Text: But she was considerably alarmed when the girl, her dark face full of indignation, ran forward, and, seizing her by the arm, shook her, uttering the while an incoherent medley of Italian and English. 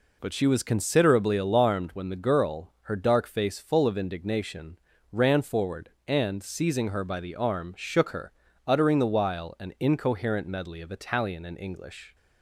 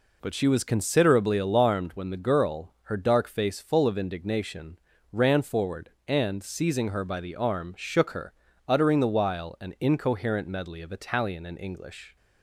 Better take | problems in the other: neither | none

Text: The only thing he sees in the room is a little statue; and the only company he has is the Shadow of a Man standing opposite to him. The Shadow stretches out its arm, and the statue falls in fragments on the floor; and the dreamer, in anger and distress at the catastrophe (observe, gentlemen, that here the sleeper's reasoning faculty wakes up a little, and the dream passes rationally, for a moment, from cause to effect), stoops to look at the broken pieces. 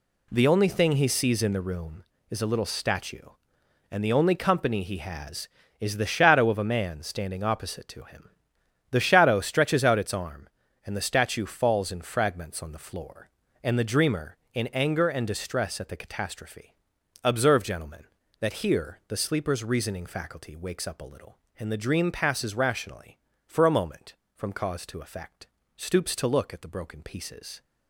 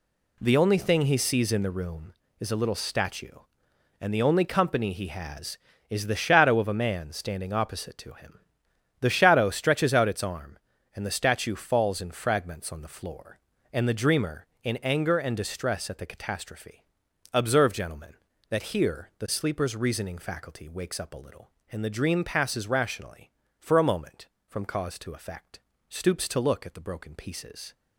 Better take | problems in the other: neither | none

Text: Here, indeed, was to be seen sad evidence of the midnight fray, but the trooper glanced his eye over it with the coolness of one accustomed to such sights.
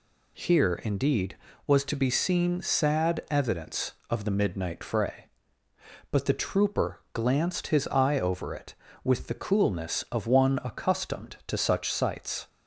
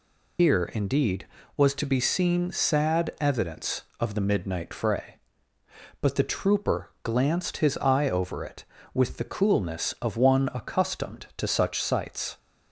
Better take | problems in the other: first | loses the start of "Here"; at 0.3 s; 140 ms

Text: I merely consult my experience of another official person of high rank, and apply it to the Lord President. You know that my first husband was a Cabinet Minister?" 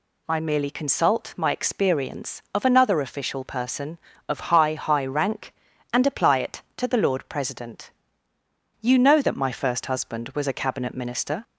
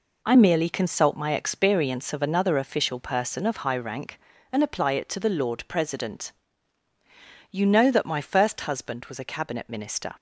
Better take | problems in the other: second | says "high" twice; at 4.7 s

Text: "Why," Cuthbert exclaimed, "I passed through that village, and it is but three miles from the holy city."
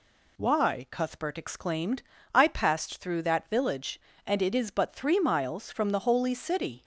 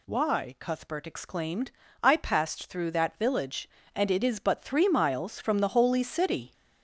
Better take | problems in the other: first | gets louder; noticeable; throughout; 5 dB

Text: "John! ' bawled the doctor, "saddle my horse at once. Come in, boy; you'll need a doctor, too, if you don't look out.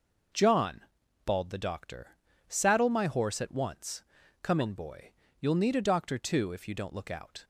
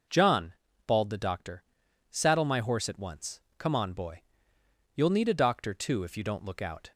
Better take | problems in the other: first | says "on" for "in"; at 3.7 s

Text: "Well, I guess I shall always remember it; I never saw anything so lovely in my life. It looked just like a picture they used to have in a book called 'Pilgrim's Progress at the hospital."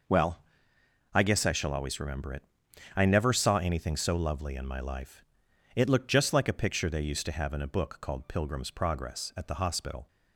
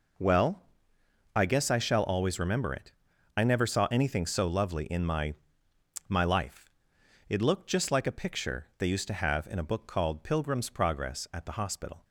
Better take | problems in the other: first | says "my" twice; at 6.0 s

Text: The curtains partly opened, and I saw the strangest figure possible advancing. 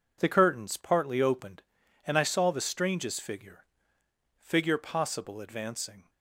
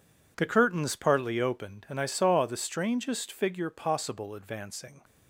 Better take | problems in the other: second | says "figure" twice; at 4.3 s

